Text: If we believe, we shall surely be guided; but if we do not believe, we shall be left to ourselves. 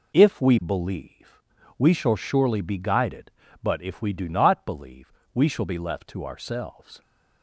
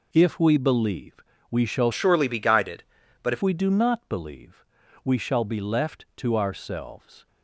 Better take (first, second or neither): first